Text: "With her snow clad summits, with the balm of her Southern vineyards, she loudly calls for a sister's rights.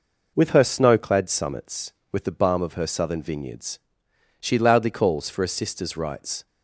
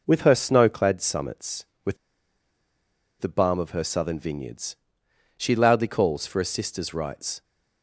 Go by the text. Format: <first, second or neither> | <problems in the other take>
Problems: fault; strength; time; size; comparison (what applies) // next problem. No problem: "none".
first | pauses between "with" and "the"; at 1.9 s; 1.2 s long